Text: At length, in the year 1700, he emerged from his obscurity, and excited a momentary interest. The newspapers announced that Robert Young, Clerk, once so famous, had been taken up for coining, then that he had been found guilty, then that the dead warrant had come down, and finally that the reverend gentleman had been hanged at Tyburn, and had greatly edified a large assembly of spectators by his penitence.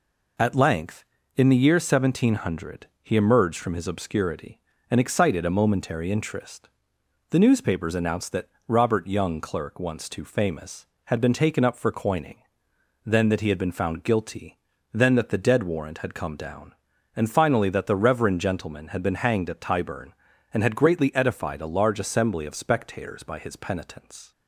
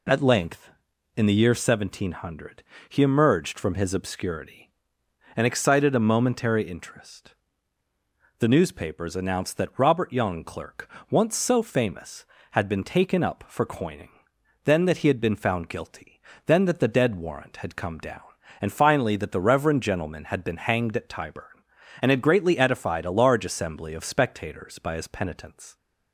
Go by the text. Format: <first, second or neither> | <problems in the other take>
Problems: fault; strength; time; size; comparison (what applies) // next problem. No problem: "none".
second | pauses between "that" and "Robert"; slight; at 8.4 s; 0.18 s long // says "too" for "so"; at 10.0 s